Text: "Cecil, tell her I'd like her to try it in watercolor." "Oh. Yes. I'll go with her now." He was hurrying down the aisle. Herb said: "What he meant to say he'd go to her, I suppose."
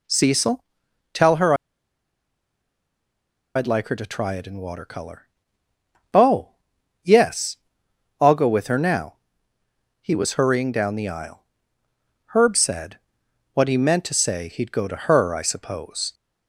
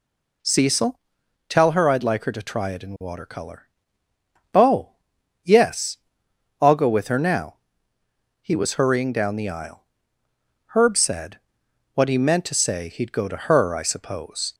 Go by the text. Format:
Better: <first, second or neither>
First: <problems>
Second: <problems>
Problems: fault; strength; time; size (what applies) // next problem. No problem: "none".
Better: second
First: pauses between "her" and "I'd"; strong; at 1.5 s; 2.0 s long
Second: none